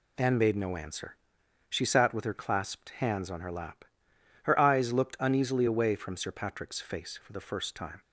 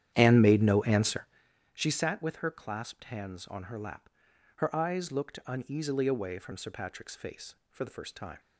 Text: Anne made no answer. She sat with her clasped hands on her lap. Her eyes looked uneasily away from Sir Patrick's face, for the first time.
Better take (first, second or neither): first